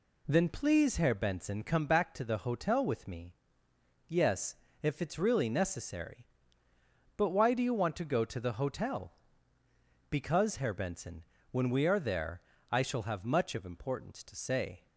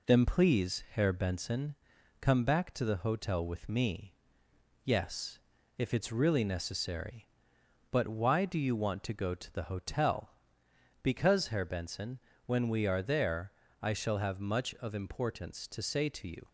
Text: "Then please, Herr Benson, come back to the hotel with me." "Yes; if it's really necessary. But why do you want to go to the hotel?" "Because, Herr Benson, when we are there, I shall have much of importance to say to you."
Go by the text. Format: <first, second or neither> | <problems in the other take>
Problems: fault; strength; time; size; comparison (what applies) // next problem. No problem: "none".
second | stops before "to you"; at 14.8 s